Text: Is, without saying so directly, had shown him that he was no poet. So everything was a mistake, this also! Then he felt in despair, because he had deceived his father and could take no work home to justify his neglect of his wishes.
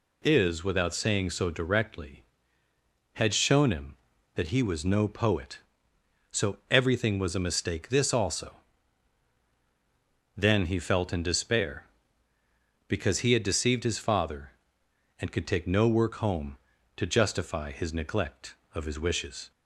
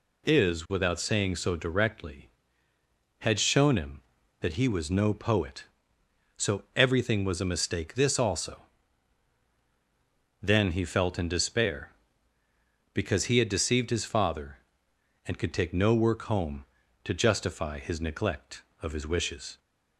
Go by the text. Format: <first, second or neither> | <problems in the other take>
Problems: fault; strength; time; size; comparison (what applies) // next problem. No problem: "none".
neither | none